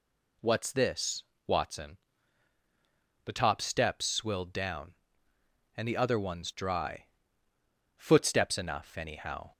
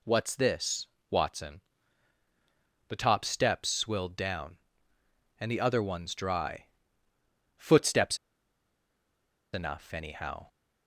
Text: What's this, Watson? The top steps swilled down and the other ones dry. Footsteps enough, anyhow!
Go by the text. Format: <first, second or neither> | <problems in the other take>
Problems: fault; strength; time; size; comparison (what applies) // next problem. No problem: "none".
first | pauses between "Footsteps" and "enough"; strong; at 8.1 s; 1.3 s long